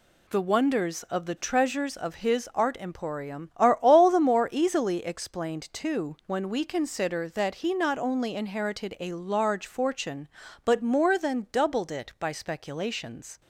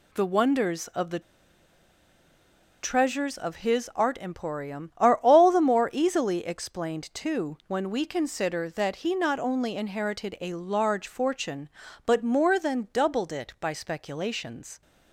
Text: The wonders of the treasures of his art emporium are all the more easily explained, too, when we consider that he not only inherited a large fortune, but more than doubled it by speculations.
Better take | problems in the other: first | pauses between "the" and "treasures"; strong; at 1.1 s; 1.6 s long

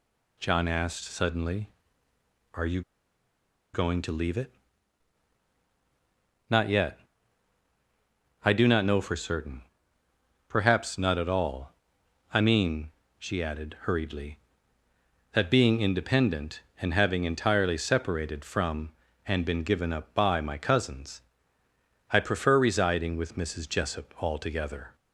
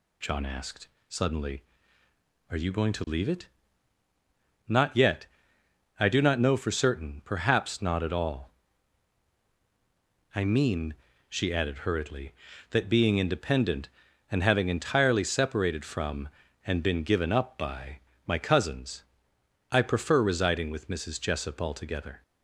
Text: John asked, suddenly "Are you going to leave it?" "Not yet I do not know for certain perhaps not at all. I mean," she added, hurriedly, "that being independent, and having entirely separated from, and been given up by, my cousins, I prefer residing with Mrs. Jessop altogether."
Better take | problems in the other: second | pauses between "you" and "going"; noticeable; at 2.8 s; 0.91 s long // pauses between "yet" and "I"; strong; at 6.9 s; 1.4 s long; noticeable in the second // pauses between "certain" and "perhaps"; noticeable; at 9.6 s; 0.84 s long

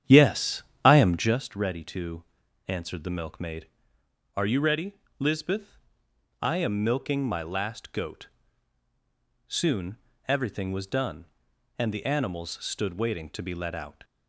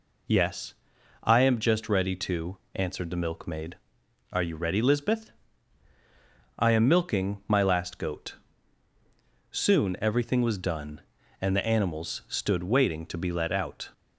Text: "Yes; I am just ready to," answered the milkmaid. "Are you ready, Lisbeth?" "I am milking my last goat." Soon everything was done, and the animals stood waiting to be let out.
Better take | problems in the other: second | starts louder than the rest; strong; until 1.5 s; 9.5 dB // pauses between "Soon" and "everything"; slight; at 9.9 s; 0.32 s long

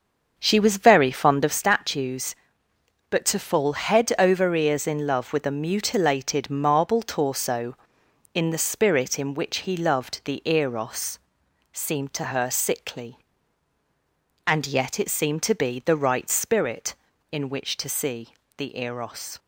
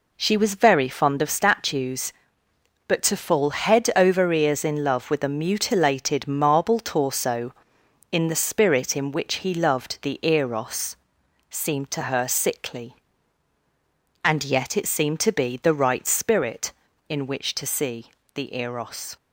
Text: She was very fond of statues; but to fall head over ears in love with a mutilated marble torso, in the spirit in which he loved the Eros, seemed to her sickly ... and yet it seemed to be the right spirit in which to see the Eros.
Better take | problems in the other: second | starts louder than the rest; until 1.6 s; 6.5 dB // pauses between "see" and "the"; slight; at 18.3 s; 0.22 s long; slight in the second

